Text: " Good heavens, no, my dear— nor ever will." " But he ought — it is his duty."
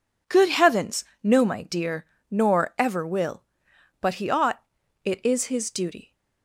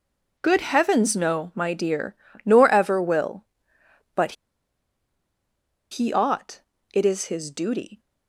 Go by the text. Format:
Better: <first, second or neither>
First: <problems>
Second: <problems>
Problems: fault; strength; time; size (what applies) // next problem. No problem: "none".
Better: first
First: none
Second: pauses between "But" and "he"; strong; at 4.3 s; 1.5 s long